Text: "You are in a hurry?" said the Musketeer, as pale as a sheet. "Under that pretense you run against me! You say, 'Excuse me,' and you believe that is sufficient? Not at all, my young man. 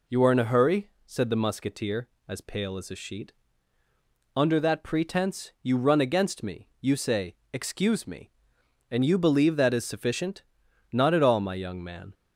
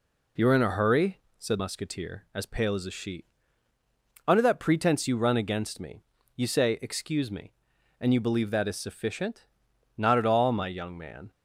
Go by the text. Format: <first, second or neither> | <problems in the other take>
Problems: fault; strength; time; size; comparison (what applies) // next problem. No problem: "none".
first | skips "the"; at 1.5 s